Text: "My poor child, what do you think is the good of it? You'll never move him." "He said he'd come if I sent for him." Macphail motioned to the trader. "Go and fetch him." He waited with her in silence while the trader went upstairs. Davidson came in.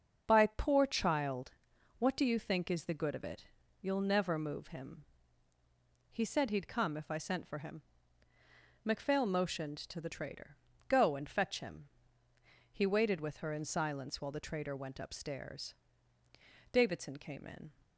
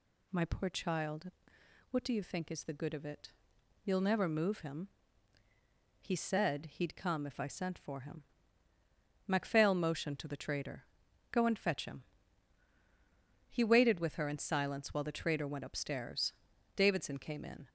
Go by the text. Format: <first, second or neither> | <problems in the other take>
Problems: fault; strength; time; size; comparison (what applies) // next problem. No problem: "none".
second | starts louder than the rest; until 1.2 s; 6.5 dB // says "By" for "My"; at 0.2 s